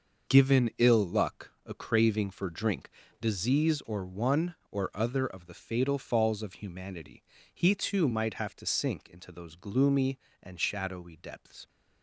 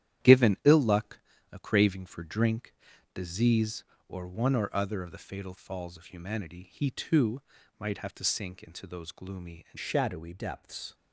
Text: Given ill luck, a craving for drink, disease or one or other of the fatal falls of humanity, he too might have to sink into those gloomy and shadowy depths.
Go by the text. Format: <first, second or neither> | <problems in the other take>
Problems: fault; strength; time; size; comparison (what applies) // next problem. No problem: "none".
first | starts louder than the rest; strong; until 1.6 s; 11.5 dB // pauses between "too" and "might"; at 7.4 s; 0.38 s long // changes voice at "shadowy"; from 9.7 s on; 1.2 s long